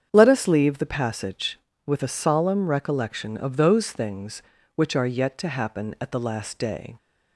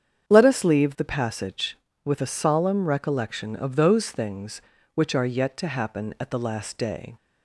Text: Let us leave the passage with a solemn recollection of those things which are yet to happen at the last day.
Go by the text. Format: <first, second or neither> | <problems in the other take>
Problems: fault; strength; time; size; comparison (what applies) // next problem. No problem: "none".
neither | starts louder than the rest; strong; the same in both